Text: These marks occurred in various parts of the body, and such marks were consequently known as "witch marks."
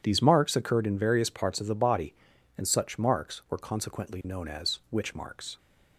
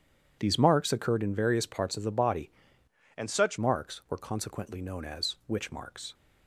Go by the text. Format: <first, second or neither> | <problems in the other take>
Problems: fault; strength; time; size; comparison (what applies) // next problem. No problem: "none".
first | changes voice from "and" to "such"; from 3.1 to 3.5 s; 0.4 s long